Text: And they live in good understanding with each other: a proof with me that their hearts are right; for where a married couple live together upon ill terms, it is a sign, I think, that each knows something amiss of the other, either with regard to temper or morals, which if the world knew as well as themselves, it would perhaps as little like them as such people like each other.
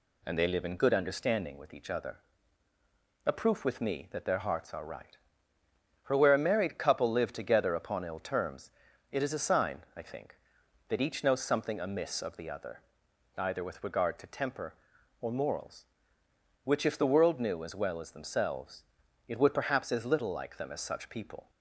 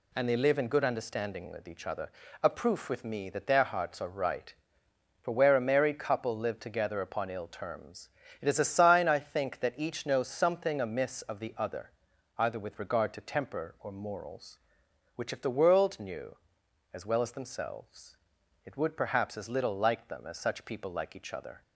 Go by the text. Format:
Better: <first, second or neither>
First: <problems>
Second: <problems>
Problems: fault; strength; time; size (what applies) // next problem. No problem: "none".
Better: second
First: stops before "like each other"; at 21.4 s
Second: none